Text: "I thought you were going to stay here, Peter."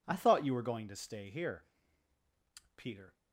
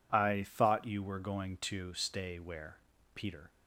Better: first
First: none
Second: says "where" for "here"; at 2.3 s

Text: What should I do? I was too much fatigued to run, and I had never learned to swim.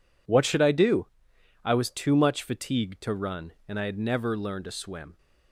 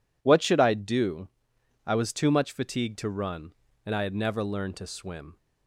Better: neither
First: none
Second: none

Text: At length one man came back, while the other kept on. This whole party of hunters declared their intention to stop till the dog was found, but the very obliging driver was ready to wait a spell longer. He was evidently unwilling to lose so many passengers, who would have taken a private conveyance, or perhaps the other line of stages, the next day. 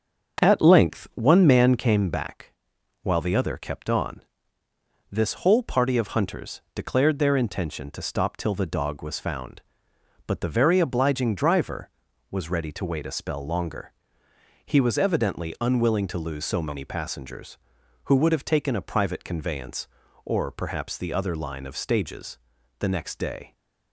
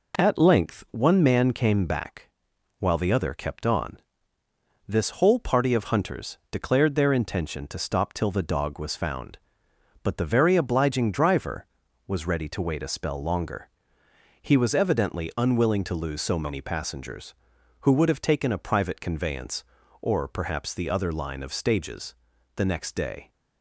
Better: second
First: starts louder than the rest; until 2.0 s; 7 dB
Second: none

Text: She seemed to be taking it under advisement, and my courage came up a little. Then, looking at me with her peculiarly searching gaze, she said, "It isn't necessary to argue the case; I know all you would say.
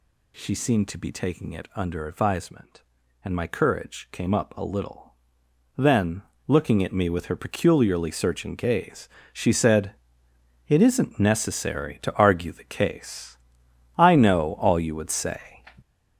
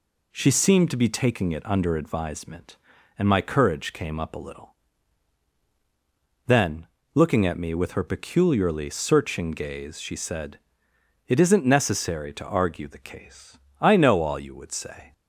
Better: second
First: gets louder; strong; throughout; 7 dB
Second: none

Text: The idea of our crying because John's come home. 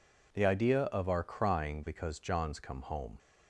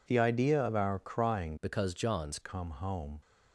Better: first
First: none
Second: changes voice from "because" to "John's"; from 1.6 to 2.4 s; 0.8 s long

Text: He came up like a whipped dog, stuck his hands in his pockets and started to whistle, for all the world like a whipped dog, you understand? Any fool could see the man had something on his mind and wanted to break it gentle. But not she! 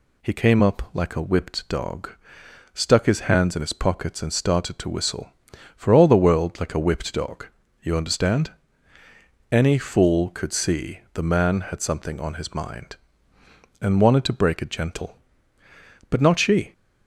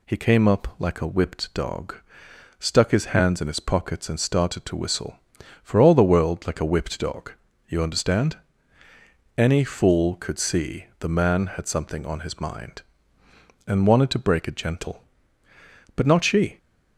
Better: neither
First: none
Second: none

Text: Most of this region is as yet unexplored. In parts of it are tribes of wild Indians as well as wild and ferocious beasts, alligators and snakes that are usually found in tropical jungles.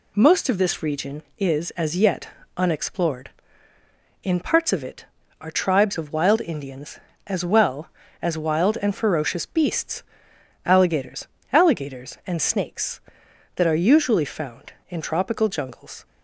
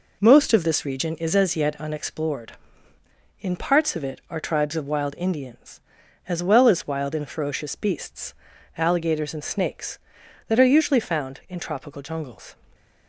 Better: second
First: pauses between "yet" and "unexplored"; slight; at 2.2 s; 0.30 s long // says "alligators" twice; at 11.5 s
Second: none

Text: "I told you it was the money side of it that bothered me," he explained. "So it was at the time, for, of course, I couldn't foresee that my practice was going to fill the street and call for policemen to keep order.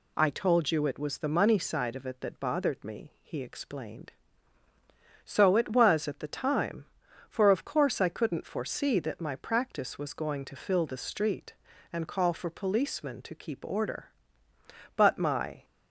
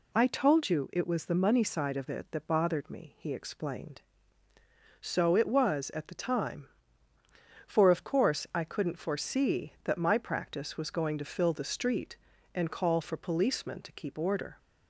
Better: second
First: goes on to say "But my"; noticeable; from 14.9 s on; 0.68 s long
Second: none

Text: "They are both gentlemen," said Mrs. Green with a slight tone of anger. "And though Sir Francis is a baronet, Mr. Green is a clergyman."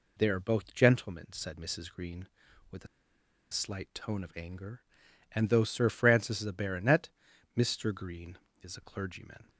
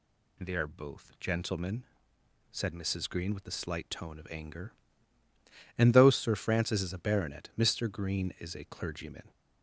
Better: second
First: pauses between "a" and "slight"; noticeable; at 2.8 s; 0.66 s long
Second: none

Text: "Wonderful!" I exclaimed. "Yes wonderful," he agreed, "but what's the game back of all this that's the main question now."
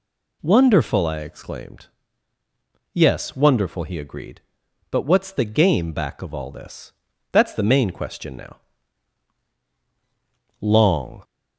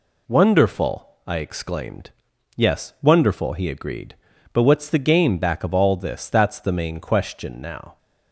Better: second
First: pauses between "this" and "that's"; at 6.9 s; 0.40 s long // goes on to say "Long"; noticeable; from 10.6 s on; 0.62 s long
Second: none

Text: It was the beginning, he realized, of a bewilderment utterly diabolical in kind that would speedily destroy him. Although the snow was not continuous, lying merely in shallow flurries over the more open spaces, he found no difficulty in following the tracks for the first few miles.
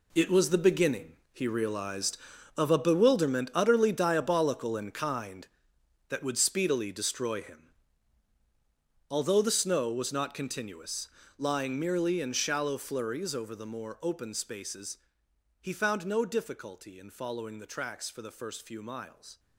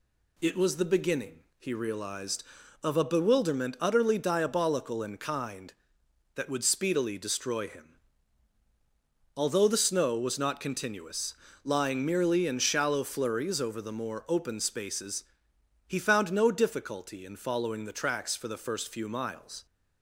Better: second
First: gets quieter; strong; throughout; 12 dB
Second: none

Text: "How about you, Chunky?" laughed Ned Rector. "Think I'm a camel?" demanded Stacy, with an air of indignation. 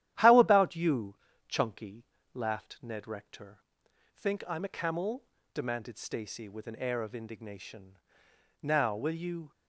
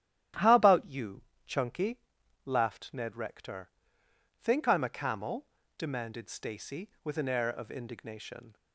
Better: second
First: starts louder than the rest; strong; until 1.4 s; 12 dB // goes on to say "Now will you"; noticeable; from 8.6 s on; 0.88 s long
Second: starts louder than the rest; strong; until 1.6 s; 12 dB

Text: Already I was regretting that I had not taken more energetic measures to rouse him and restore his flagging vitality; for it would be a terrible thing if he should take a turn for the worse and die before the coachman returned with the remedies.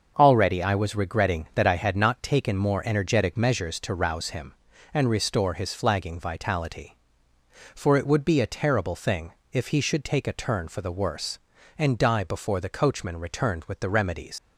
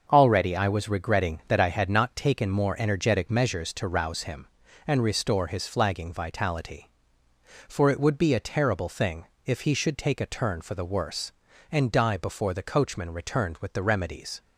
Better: second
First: starts louder than the rest; until 1.1 s; 6.5 dB // pauses between "thing" and "if"; slight; at 9.3 s; 0.18 s long // leaves "remedies" unfinished; at 14.3 s; 85 ms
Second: starts louder than the rest; until 1.1 s; 6.5 dB // pauses between "thing" and "if"; slight; at 9.2 s; 0.18 s long

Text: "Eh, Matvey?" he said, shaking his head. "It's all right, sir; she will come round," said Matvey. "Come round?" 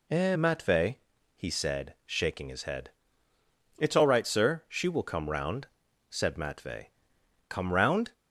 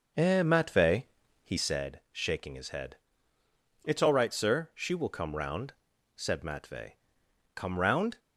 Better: first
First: none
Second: starts louder than the rest; until 1.8 s; 6.5 dB

